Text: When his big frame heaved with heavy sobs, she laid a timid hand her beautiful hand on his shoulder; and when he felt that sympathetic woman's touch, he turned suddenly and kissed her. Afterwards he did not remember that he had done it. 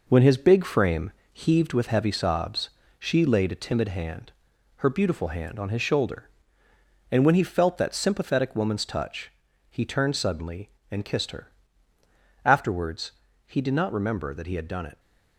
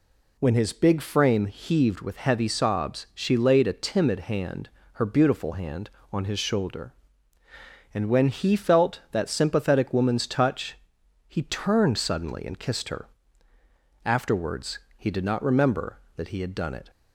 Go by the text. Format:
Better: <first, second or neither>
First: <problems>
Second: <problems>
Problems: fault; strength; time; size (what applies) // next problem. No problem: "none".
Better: second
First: gets quieter; noticeable; throughout; 6 dB // pauses between "frame" and "heaved"; slight; at 1.1 s; 0.22 s long // pauses between "hand" and "her"; noticeable; at 4.3 s; 0.50 s long // pauses between "Afterwards" and "he"; slight; at 13.1 s; 0.34 s long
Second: pauses between "hand" and "her"; slight; at 4.6 s; 0.24 s long // pauses between "Afterwards" and "he"; slight; at 14.8 s; 0.16 s long